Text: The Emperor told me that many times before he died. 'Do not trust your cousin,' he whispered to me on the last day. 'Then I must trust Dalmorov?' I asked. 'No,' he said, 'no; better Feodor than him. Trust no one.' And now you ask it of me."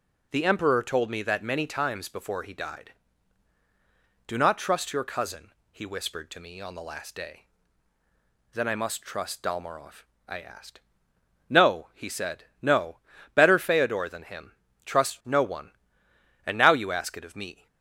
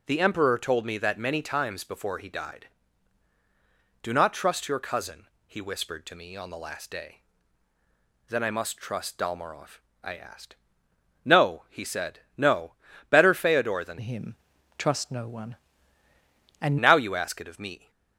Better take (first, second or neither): first